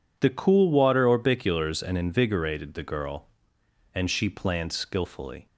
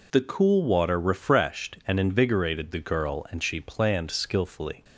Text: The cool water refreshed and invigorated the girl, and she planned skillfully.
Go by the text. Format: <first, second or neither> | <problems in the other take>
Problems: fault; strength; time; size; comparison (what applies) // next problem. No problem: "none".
second | says "orbiculars" for "refreshed"; at 1.0 s